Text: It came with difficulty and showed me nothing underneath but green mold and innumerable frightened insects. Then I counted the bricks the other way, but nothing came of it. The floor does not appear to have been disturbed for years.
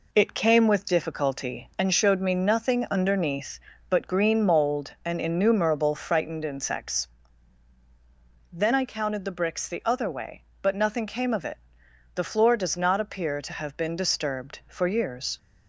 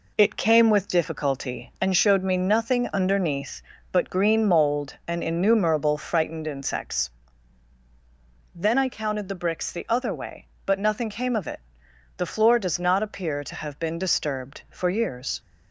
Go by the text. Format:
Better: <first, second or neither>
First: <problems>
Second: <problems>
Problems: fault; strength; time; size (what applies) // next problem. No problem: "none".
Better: neither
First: none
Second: none